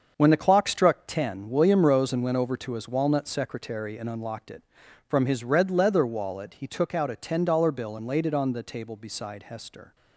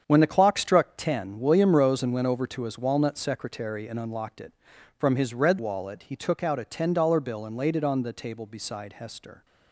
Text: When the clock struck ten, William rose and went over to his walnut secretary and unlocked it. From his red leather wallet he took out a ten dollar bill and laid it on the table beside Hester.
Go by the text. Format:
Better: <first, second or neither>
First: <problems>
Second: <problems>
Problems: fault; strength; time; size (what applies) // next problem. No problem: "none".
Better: first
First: starts louder than the rest; until 1.1 s; 6.5 dB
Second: starts louder than the rest; strong; until 1.0 s; 8 dB // skips "leather"; at 5.5 s